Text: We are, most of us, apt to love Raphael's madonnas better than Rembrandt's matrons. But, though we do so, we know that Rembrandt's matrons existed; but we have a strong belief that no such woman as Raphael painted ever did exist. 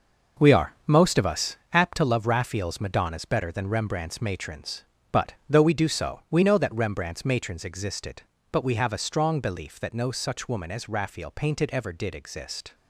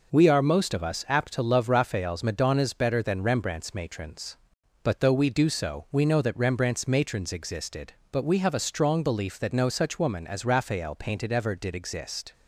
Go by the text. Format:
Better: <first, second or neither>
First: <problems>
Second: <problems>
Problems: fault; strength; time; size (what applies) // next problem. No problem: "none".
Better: second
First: gets quieter; strong; throughout; 9 dB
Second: none